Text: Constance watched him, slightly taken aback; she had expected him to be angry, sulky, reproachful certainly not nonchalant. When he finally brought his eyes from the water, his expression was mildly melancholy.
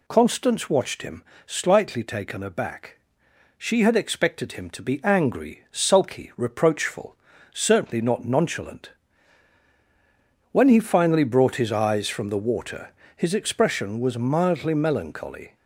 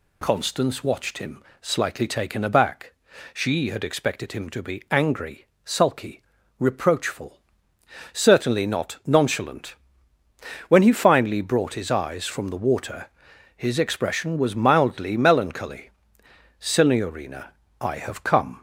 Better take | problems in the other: first | pauses between "reproachful" and "certainly"; noticeable; at 7.4 s; 0.72 s long; slight in the first // goes on to say "Signorina I have come"; strong; from 16.6 s on; 2.0 s long

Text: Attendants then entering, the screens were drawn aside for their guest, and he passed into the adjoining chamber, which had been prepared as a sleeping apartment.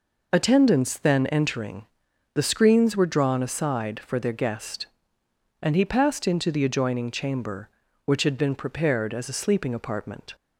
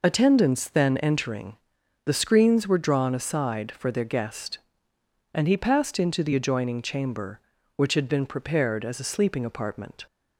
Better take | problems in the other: neither | none

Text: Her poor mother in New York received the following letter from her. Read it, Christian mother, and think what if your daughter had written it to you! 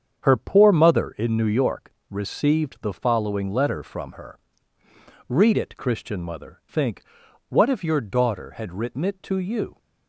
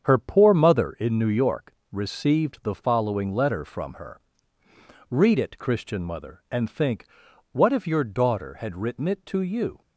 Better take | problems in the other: second | starts louder than the rest; strong; until 1.2 s; 7.5 dB; strong in the second // pauses between "York" and "received"; slight; at 1.9 s; 0.16 s long; slight in the second // skips "and"; at 6.6 s // pauses between "think" and "what"; noticeable; at 7.0 s; 0.46 s long; noticeable in the second

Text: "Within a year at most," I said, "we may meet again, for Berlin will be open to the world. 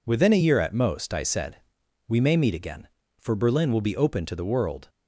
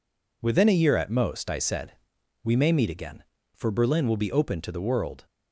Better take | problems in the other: neither | none

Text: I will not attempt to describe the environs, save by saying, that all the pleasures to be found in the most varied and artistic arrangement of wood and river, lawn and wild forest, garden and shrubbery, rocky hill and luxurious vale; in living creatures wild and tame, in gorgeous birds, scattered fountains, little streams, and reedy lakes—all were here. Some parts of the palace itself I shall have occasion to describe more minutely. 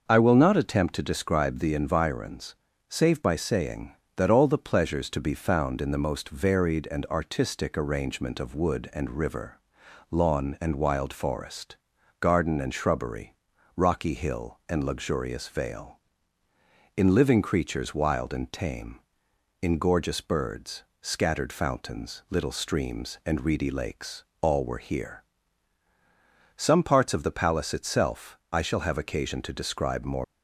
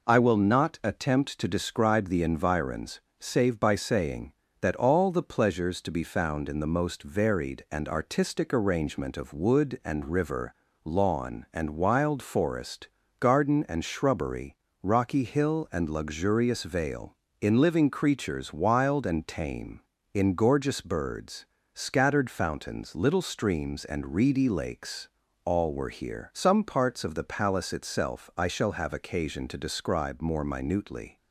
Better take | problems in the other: second | stops before "minutely"; at 30.2 s

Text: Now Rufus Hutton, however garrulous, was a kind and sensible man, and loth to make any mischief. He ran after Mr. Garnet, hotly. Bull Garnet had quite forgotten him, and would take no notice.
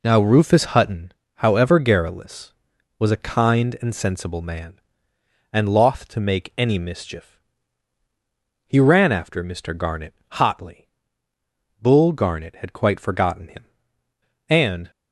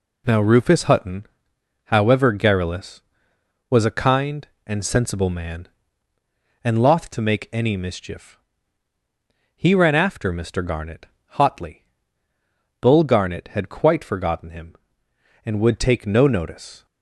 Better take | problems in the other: second | stops before "would take no notice"; at 14.9 s

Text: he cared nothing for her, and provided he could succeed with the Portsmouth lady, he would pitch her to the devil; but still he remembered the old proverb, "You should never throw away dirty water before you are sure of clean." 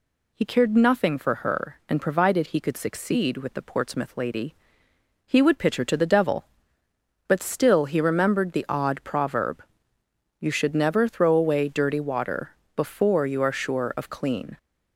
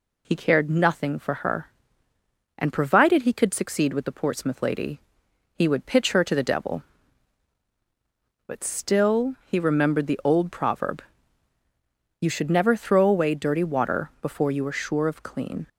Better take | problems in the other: second | says "odd" for "old"; at 8.6 s // pauses between "water" and "before"; slight; at 12.5 s; 0.20 s long

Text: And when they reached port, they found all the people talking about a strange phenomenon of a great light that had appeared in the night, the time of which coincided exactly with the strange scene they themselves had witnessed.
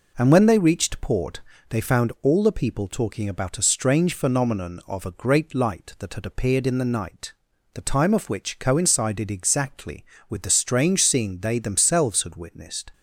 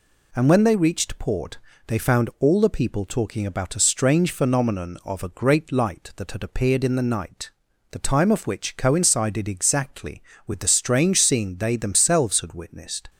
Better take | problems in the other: second | starts louder than the rest; noticeable; until 1.8 s; 4.5 dB

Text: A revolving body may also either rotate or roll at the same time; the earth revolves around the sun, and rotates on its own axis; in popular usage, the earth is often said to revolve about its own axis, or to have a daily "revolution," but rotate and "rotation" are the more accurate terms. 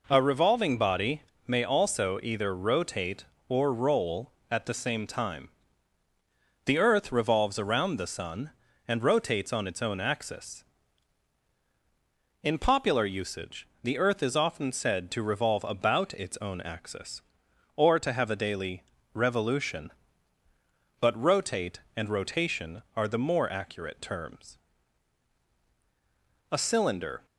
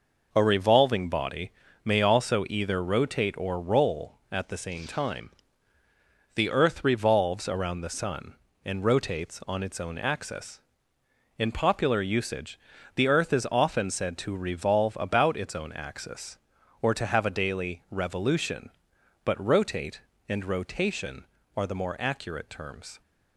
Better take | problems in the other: second | pauses between "body" and "may"; slight; at 1.2 s; 0.24 s long; slight in the second // pauses between "daily" and "revolution"; slight; at 18.8 s; 0.32 s long // goes on to say "A cylinder"; noticeable; from 26.5 s on; 0.74 s long

